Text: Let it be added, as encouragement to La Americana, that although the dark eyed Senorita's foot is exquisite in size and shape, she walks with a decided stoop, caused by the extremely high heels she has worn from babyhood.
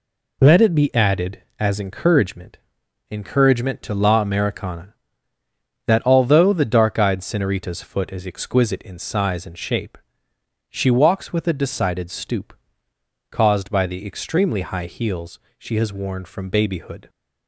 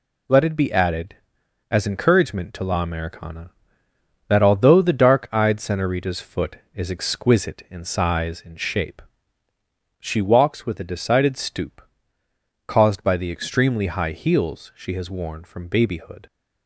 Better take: second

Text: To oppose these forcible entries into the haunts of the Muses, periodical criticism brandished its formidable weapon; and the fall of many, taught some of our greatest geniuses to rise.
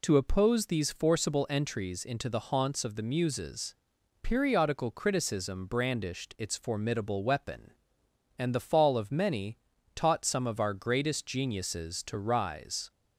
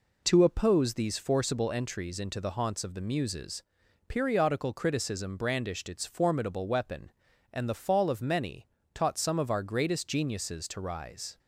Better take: neither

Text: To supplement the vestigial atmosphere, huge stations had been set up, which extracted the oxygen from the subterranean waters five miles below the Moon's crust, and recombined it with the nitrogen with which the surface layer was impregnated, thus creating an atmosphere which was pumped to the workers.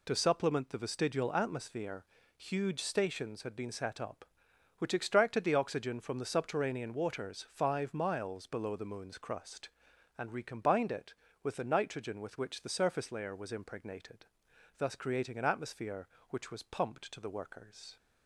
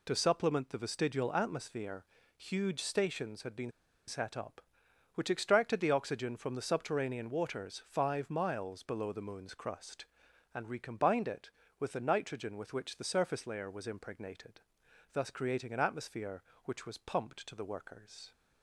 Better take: first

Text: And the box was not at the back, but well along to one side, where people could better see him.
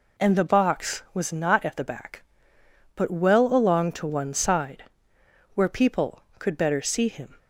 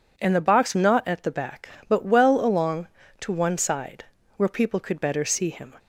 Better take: first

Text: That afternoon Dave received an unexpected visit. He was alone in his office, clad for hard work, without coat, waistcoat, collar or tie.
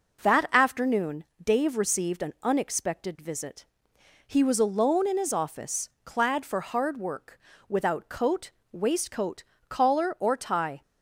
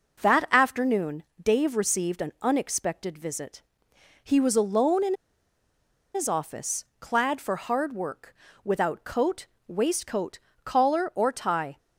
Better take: first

